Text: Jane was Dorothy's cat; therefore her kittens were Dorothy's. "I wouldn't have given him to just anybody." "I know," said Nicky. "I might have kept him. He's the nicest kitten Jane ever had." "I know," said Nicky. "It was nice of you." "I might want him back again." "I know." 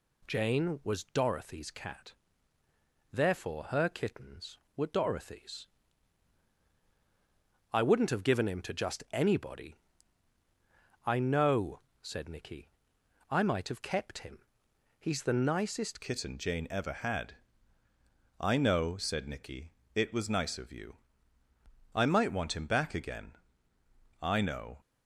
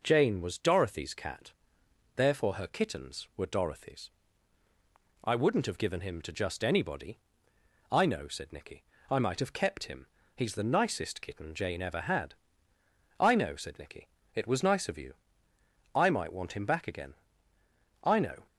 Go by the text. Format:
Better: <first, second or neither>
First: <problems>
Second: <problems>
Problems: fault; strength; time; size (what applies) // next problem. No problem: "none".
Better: second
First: changes voice at "kitten"; from 16.0 s on; 8.7 s long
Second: none